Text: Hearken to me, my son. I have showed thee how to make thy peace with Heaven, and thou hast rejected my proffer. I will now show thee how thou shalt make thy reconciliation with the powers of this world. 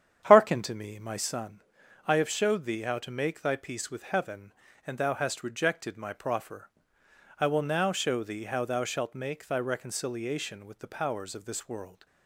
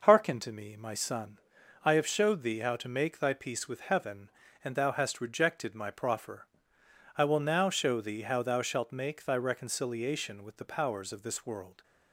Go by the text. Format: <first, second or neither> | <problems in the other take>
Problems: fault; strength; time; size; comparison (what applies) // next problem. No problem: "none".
second | starts louder than the rest; strong; until 1.3 s; 9 dB